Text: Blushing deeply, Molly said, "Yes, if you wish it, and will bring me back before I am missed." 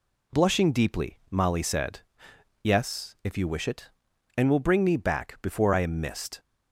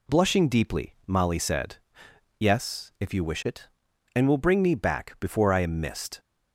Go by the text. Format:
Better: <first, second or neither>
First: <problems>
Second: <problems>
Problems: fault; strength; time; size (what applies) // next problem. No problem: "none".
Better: neither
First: none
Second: none